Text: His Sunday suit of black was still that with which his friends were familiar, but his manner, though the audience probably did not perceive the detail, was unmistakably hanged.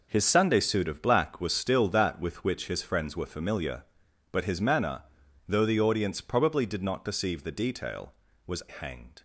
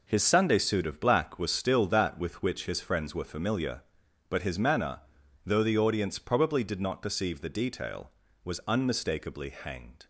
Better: second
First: skips "unmistakably"; at 8.6 s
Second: none

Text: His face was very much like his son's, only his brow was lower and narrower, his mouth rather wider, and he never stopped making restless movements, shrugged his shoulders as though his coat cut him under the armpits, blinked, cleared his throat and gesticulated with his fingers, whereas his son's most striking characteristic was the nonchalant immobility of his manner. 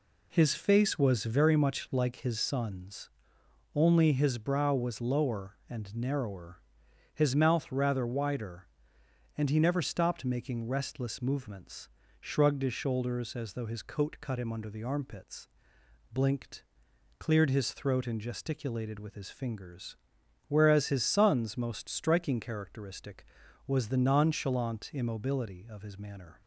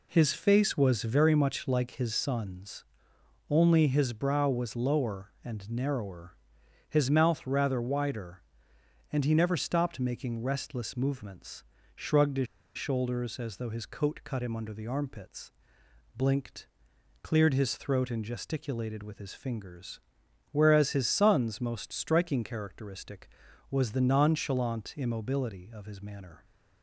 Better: first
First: none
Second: pauses between "his" and "shoulders"; slight; at 12.4 s; 0.29 s long

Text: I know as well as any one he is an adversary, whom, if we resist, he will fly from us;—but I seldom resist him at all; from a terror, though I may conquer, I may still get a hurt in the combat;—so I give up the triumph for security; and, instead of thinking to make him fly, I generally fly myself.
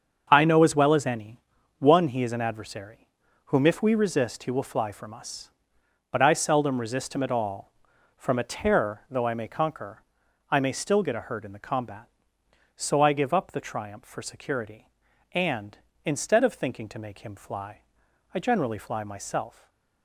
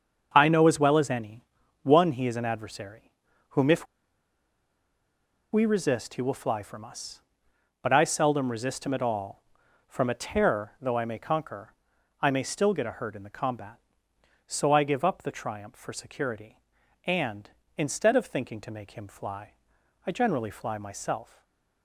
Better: first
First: starts louder than the rest; until 1.3 s; 7 dB // pauses between "any" and "one"; at 1.3 s; 0.40 s long // stays silent after the last word; slight; from 19.4 s on; 0.6 s long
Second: starts louder than the rest; until 1.3 s; 7 dB // pauses between "any" and "one"; at 1.4 s; 0.40 s long // pauses between "if" and "we"; strong; at 3.8 s; 1.6 s long // stays silent after the last word; slight; from 21.2 s on; 0.6 s long

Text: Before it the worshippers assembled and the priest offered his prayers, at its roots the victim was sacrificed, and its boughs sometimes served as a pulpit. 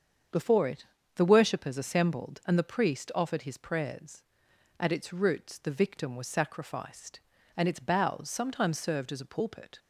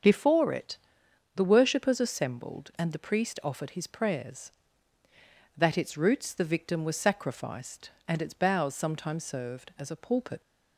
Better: first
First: starts louder than the rest; strong; until 1.6 s; 7 dB // pauses between "it" and "the"; slight; at 0.8 s; 0.30 s long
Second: starts louder than the rest; strong; until 1.6 s; 7 dB // pauses between "it" and "the"; noticeable; at 0.7 s; 0.58 s long // says "that" for "at"; at 5.5 s

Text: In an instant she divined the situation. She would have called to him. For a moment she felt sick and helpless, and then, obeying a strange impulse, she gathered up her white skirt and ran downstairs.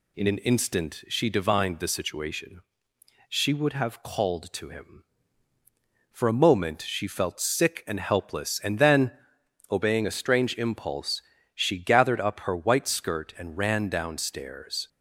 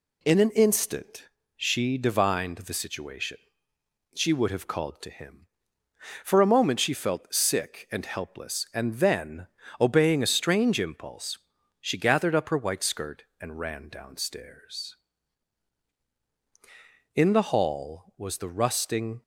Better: first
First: none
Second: pauses between "instant" and "she"; slight; at 1.2 s; 0.27 s long // goes on to say "In the hall was the rusting"; strong; from 17.1 s on; 2.0 s long

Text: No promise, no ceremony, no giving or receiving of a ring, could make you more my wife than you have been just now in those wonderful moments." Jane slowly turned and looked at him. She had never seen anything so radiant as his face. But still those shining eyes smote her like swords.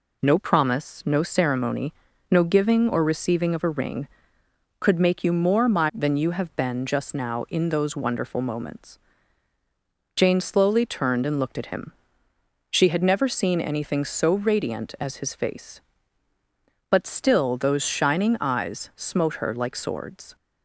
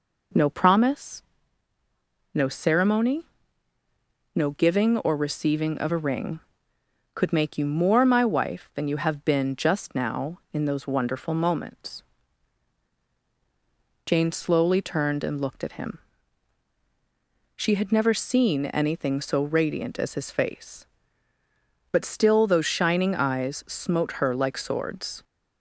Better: second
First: skips "wife"; at 5.9 s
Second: none

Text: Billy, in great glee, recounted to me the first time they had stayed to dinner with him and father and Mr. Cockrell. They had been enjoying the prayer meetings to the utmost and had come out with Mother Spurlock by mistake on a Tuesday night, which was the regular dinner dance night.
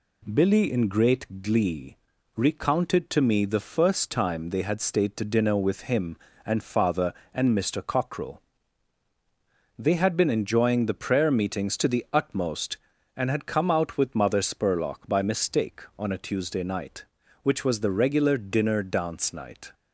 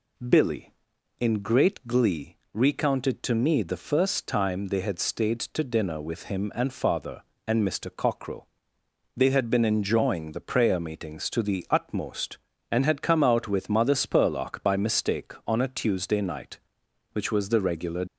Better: first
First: none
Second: stops before "dinner dance night"; at 18.0 s

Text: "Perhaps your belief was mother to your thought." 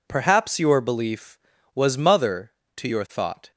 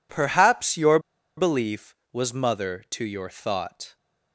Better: first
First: none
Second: pauses between "your" and "belief"; at 0.9 s; 0.38 s long

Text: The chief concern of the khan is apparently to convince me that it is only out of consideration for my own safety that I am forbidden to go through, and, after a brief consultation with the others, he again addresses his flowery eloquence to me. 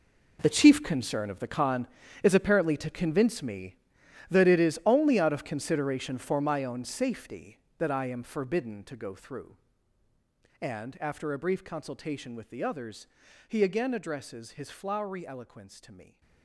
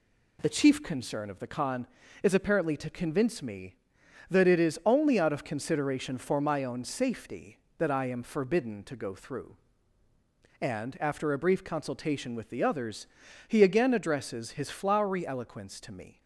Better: second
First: gets quieter; strong; throughout; 15.5 dB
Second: none

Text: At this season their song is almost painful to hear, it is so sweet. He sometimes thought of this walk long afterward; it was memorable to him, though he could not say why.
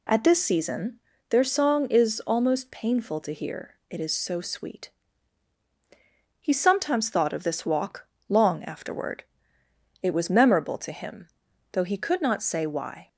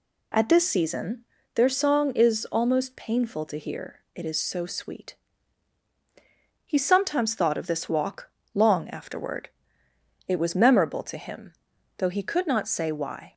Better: neither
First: pauses between "season" and "their"; slight; at 0.9 s; 0.32 s long // pauses between "walk" and "long"; slight; at 8.0 s; 0.21 s long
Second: pauses between "season" and "their"; slight; at 1.2 s; 0.32 s long // pauses between "walk" and "long"; slight; at 8.2 s; 0.24 s long

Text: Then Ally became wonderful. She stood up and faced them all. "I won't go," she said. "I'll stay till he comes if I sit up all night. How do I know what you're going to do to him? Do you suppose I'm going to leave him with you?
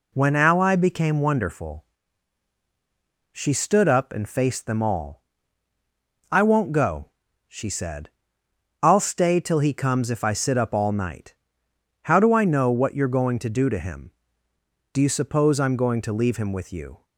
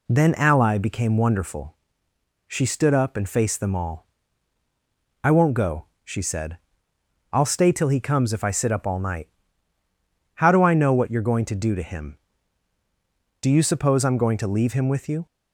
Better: second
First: says "When" for "Then"; at 0.1 s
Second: none

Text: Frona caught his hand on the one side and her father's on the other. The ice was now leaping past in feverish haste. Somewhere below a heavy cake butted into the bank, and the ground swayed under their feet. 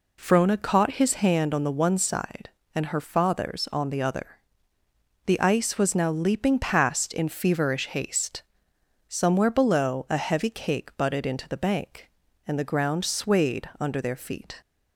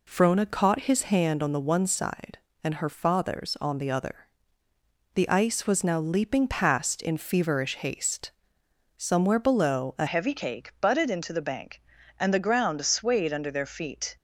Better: first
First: none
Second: changes voice at "heavy"; from 10.0 s on; 4.1 s long

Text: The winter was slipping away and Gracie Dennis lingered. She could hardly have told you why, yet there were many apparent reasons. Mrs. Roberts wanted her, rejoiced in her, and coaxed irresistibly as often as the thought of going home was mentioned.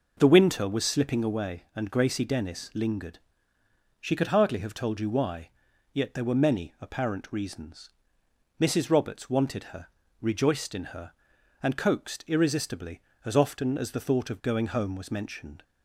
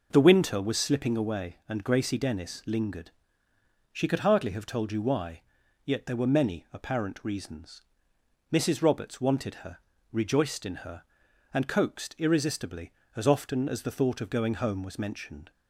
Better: neither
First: none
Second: none

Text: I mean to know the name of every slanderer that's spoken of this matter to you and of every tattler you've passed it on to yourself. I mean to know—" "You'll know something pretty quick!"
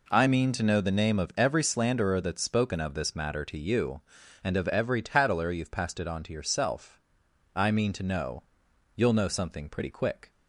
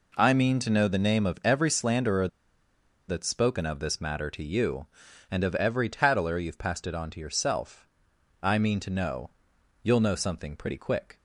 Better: first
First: none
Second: pauses between "slanderer" and "that's"; noticeable; at 2.2 s; 0.81 s long

